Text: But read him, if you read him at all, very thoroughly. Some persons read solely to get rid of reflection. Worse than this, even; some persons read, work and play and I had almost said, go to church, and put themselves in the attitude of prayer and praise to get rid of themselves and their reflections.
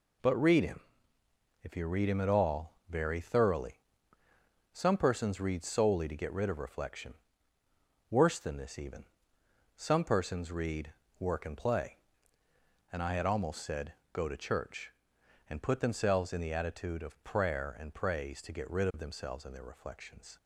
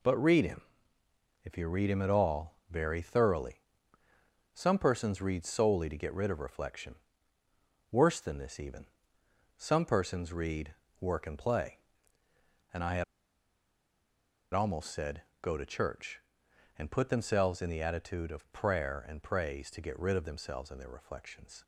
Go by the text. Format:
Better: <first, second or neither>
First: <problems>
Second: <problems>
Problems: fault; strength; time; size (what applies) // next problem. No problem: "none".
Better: first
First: none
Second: pauses between "had" and "almost"; strong; at 13.0 s; 1.4 s long